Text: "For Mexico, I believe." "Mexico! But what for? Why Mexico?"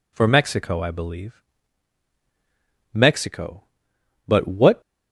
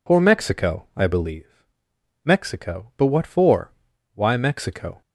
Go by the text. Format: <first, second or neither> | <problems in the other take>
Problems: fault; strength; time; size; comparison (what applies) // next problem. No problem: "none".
second | stops before "for Why Mexico"; at 4.8 s